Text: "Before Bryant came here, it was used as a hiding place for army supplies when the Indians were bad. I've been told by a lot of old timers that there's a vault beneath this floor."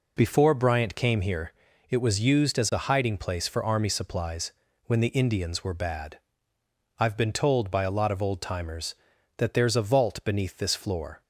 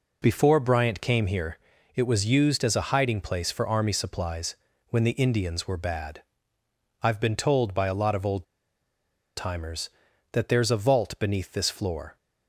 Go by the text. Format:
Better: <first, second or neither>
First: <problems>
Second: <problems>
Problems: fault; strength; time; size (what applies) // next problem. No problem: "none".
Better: first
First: pauses between "supplies" and "when"; slight; at 4.5 s; 0.32 s long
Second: pauses between "supplies" and "when"; slight; at 4.5 s; 0.32 s long // pauses between "old" and "timers"; noticeable; at 8.4 s; 0.91 s long